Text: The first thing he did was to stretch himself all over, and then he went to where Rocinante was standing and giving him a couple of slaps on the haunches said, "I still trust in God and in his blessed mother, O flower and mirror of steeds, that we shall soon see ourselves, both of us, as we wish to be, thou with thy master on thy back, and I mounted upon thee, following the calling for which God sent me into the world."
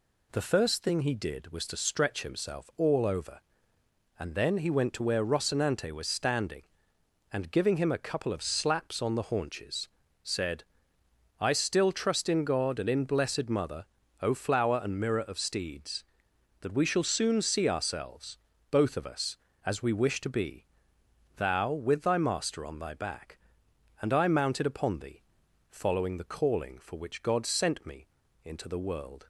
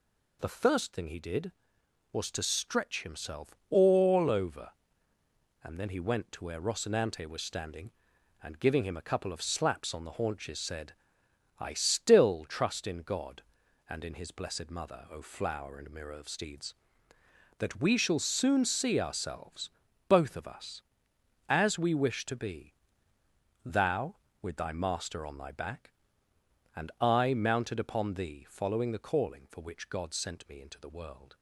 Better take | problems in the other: second | pauses between "haunches" and "said"; slight; at 9.8 s; 0.34 s long // skips "his"; at 13.0 s // pauses between "me" and "into"; at 28.0 s; 0.38 s long

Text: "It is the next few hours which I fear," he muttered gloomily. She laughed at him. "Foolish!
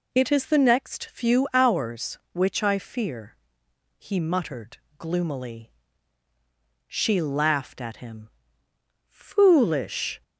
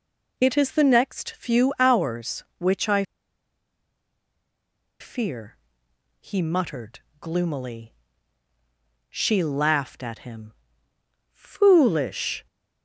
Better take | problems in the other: first | pauses between "I" and "fear"; strong; at 3.0 s; 1.9 s long // pauses between "muttered" and "gloomily"; slight; at 7.0 s; 0.20 s long; slight in the first

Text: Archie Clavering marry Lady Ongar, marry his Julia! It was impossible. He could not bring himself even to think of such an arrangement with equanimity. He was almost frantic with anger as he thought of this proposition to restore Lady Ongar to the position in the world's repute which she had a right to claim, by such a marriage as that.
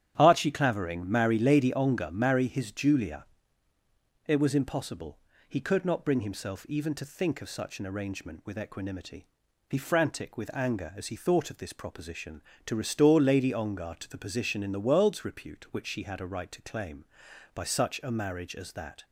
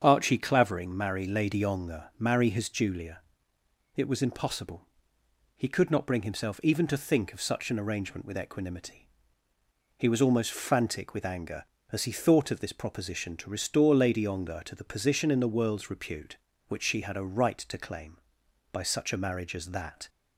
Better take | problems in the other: second | starts louder than the rest; strong; until 1.1 s; 10 dB; strong in the second // skips "was almost"; at 9.7 s

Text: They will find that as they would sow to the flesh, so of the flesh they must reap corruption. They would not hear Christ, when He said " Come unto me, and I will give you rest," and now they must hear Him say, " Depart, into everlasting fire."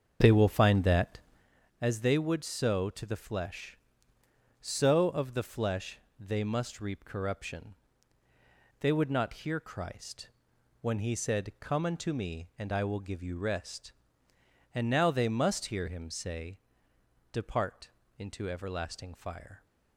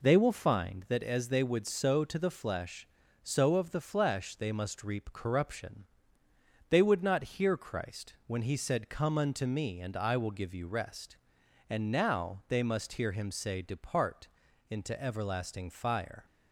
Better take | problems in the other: second | starts louder than the rest; until 1.5 s; 7 dB // pauses between "flesh" and "they"; slight; at 5.9 s; 0.22 s long

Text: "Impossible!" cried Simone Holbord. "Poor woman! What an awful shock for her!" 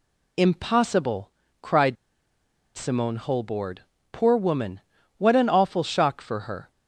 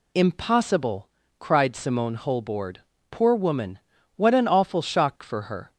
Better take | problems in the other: second | pauses between "cried" and "Simone"; noticeable; at 1.9 s; 0.80 s long

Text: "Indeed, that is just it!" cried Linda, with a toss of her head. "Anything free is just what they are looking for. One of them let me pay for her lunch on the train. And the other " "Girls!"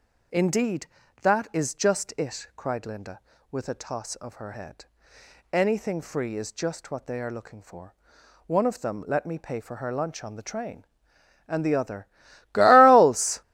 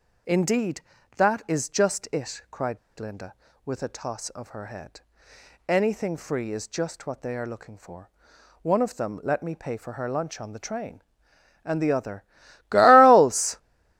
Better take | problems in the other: first | pauses between "cried" and "Linda"; slight; at 2.7 s; 0.22 s long

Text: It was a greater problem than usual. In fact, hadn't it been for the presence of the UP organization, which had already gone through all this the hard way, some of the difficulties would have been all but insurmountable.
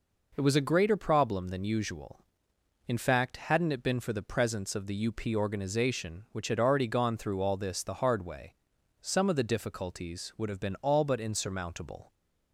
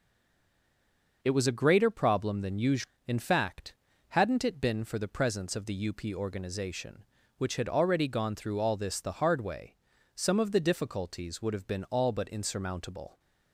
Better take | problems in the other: first | stays silent before the first word; noticeable; until 1.2 s; 1.2 s long

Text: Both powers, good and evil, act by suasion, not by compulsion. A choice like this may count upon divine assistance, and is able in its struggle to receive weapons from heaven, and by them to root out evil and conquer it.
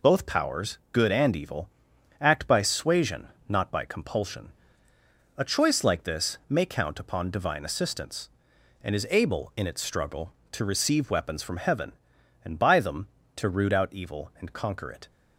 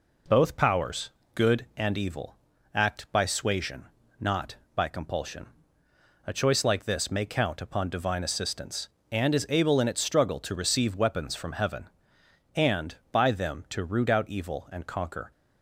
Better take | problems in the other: first | stops before "it"; at 15.3 s

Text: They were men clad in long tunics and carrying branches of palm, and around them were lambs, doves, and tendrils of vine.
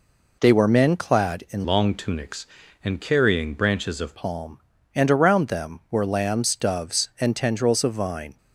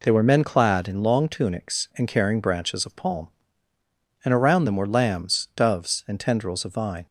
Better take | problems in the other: second | changes voice from "long" to "of"; from 1.6 to 4.1 s; 2.5 s long

